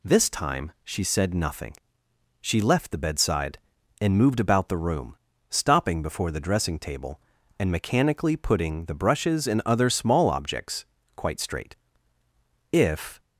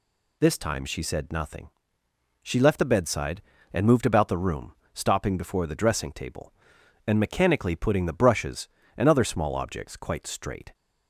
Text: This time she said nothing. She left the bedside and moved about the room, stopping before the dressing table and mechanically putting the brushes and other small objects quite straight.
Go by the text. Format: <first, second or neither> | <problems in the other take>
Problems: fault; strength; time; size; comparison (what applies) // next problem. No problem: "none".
second | pauses between "objects" and "quite"; slight; at 10.8 s; 0.30 s long // goes on to say "If"; slight; from 12.7 s on; 0.48 s long